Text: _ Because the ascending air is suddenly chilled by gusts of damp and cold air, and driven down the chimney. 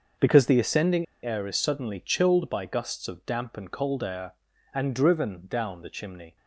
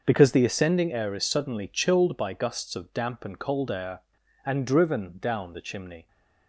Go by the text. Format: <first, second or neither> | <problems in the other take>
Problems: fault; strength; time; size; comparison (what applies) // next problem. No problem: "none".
second | starts louder than the rest; until 1.3 s; 6.5 dB; also in the second // pauses between "ascending" and "air"; slight; at 1.0 s; 0.18 s long